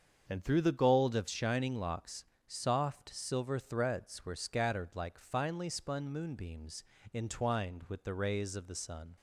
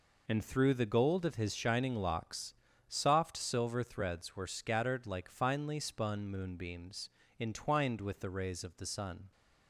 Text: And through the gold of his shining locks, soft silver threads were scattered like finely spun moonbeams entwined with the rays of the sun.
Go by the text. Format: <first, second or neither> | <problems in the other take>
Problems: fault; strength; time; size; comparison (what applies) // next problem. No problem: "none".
second | starts louder than the rest; until 1.3 s; 7 dB // skips "his"; at 1.2 s // pauses between "moonbeams" and "entwined"; slight; at 6.8 s; 0.30 s long; slight in the second